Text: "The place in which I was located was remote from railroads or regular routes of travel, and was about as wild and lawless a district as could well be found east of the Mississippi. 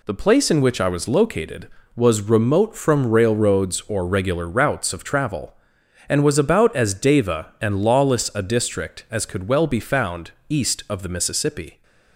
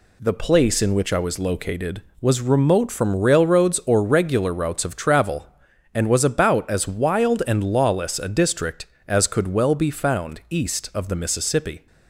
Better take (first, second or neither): second